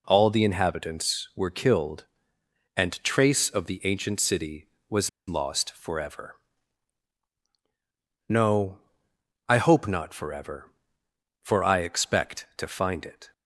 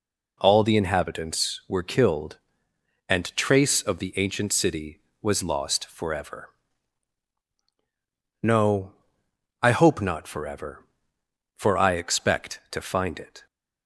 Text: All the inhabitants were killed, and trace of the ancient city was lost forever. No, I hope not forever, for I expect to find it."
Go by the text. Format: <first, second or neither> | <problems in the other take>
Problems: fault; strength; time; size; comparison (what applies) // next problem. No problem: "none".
second | pauses between "was" and "lost"; slight; at 5.0 s; 0.18 s long